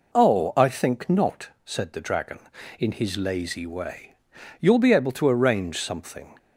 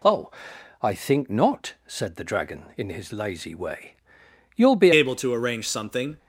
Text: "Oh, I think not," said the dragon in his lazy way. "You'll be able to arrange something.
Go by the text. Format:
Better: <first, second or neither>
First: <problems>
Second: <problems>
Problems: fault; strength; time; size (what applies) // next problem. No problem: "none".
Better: first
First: none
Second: changes voice at "able"; from 4.9 s on; 1.2 s long